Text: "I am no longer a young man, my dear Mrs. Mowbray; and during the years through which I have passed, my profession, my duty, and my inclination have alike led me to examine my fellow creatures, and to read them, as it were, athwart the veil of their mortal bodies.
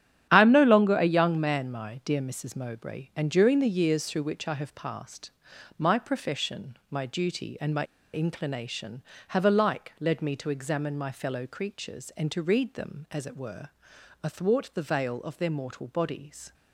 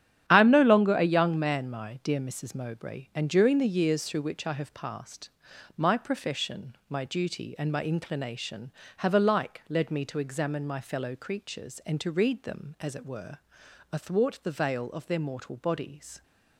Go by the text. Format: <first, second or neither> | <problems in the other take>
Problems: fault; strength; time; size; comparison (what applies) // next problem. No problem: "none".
second | starts louder than the rest; strong; until 1.3 s; 10 dB; strong in the second // pauses between "my" and "inclination"; slight; at 7.8 s; 0.27 s long